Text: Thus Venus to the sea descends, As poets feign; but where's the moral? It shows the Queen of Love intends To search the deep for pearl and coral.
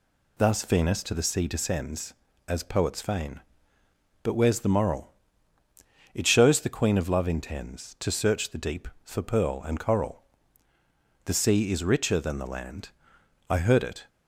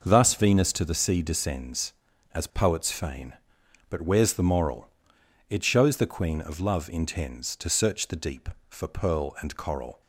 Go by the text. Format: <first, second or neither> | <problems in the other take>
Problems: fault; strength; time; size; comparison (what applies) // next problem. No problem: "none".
second | goes on to say "The sea is richer than the land I heard it"; strong; from 11.2 s on; 2.8 s long